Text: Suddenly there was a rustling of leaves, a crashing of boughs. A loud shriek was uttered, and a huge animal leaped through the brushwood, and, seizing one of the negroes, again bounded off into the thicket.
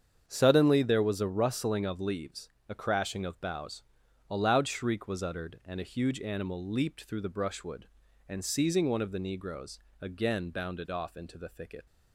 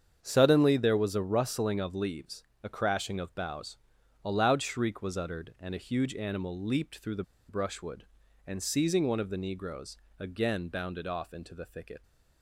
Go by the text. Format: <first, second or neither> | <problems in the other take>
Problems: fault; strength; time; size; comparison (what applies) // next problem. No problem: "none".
first | starts louder than the rest; strong; until 1.2 s; 7.5 dB; strong in the first // pauses between "the" and "brushwood"; slight; at 7.2 s; 0.26 s long